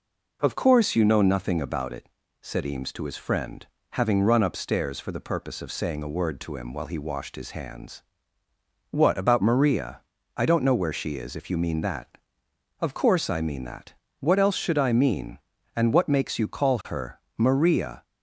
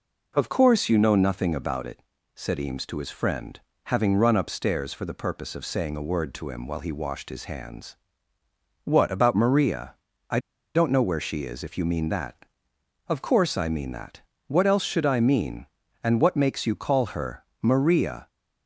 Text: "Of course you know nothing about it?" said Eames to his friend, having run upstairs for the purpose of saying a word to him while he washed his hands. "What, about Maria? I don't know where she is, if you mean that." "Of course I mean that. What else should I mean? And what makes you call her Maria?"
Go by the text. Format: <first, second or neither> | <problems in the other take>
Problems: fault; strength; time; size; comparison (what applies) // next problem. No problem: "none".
first | pauses between "I" and "don't"; slight; at 10.4 s; 0.34 s long // pauses between "her" and "Maria"; slight; at 17.4 s; 0.18 s long; slight in the first